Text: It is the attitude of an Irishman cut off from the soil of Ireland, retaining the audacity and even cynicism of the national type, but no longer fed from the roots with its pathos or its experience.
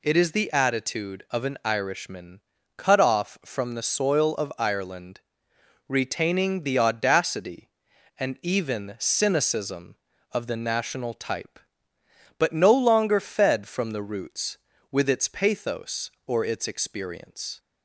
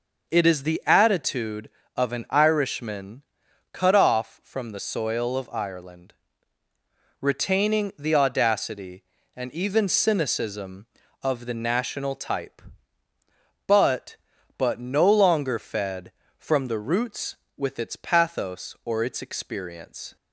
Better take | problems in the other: first | pauses between "Irishman" and "cut"; noticeable; at 3.2 s; 0.48 s long; slight in the first // says "but" twice; at 14.5 s

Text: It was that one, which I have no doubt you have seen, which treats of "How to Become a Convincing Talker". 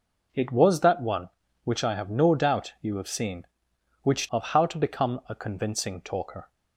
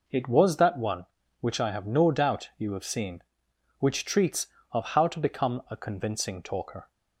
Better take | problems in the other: second | skips "treats"; at 4.2 s

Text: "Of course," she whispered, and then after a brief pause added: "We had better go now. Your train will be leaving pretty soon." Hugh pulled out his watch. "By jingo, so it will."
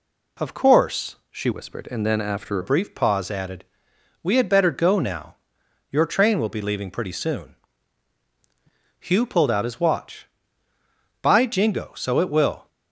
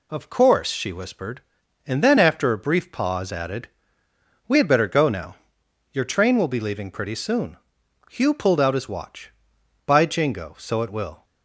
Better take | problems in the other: second | changes voice from "whispered" to "after"; from 1.5 to 2.5 s; 1.0 s long

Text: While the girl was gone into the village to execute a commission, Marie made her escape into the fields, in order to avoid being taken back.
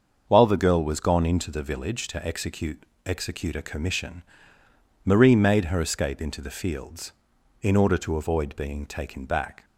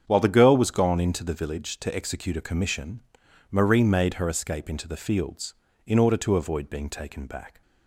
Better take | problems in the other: second | starts louder than the rest; until 1.2 s; 6.5 dB; strong in the second // says "execute" twice; at 3.0 s

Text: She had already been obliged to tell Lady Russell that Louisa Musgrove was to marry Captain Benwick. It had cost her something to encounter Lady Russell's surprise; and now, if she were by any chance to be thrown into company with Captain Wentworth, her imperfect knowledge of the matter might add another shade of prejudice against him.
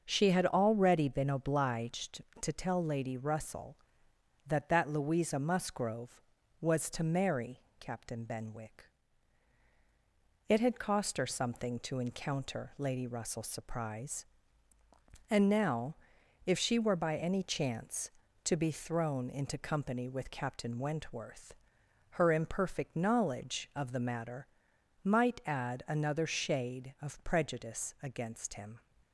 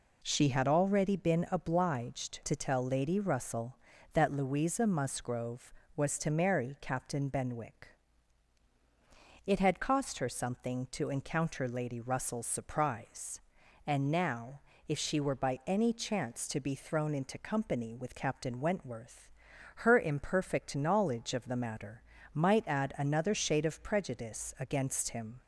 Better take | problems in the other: second | starts louder than the rest; until 1.0 s; 6 dB // says "that" twice; at 4.6 s // pauses between "marry" and "Captain"; slight; at 7.6 s; 0.18 s long // pauses between "matter" and "might"; noticeable; at 24.4 s; 0.56 s long; slight in the second

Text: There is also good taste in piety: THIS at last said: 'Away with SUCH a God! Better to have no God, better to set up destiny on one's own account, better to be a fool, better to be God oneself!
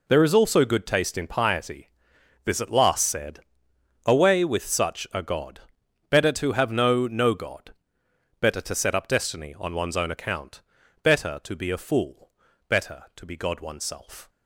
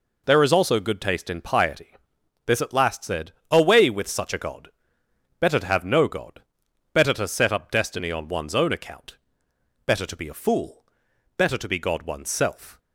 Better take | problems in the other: second | says "no" twice; at 7.0 s

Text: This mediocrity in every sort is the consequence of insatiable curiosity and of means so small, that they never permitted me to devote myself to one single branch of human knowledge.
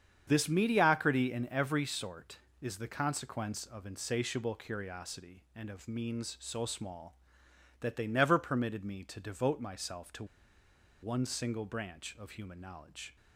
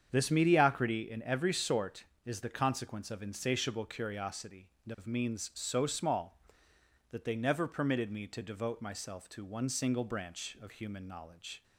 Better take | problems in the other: second | starts louder than the rest; strong; until 1.2 s; 8 dB; strong in the second // pauses between "to" and "one"; noticeable; at 10.2 s; 0.77 s long

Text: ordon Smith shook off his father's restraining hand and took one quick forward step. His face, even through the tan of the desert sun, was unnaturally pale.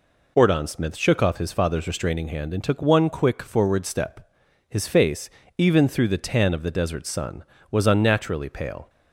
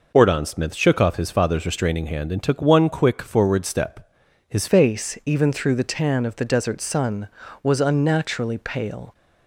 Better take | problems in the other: first | changes voice at "face"; from 4.6 s on; 4.5 s long

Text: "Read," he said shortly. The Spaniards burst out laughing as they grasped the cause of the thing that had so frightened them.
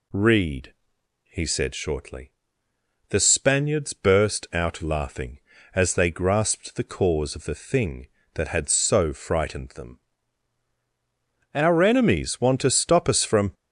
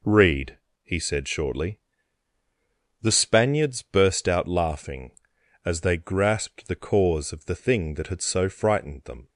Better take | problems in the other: second | goes on to say "Our enemies want to stop us from"; strong; from 11.5 s on; 2.0 s long

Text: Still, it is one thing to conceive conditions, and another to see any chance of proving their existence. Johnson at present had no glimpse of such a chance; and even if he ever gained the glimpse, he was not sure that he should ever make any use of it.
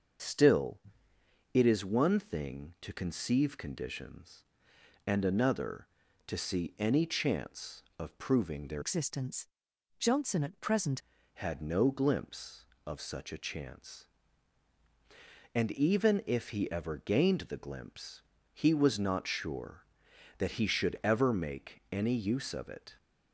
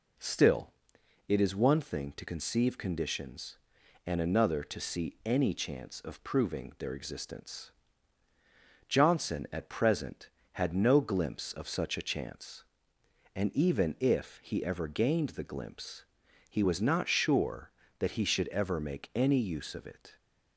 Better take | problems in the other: second | starts louder than the rest; until 1.9 s; 6.5 dB // changes voice from "existence" to "present"; from 8.8 to 10.9 s; 2.1 s long

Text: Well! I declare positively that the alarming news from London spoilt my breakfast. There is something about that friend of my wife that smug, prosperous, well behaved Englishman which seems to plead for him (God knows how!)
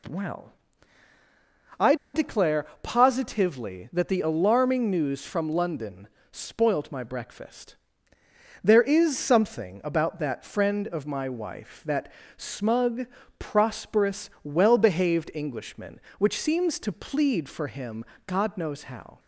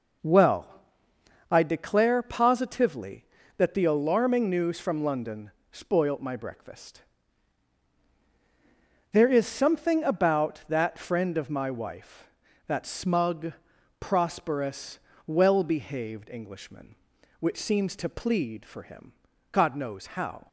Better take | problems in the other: second | pauses between "I" and "declare"; slight; at 1.9 s; 0.19 s long // pauses between "declare" and "positively"; slight; at 2.6 s; 0.18 s long // pauses between "London" and "spoilt"; slight; at 6.0 s; 0.24 s long; slight in the second // pauses between "that" and "smug"; slight; at 12.1 s; 0.26 s long

